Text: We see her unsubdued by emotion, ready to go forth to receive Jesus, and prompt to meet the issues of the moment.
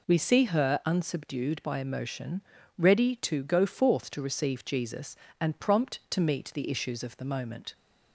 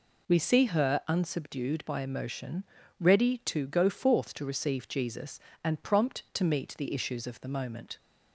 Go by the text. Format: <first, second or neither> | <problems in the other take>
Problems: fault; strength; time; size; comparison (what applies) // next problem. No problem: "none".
neither | none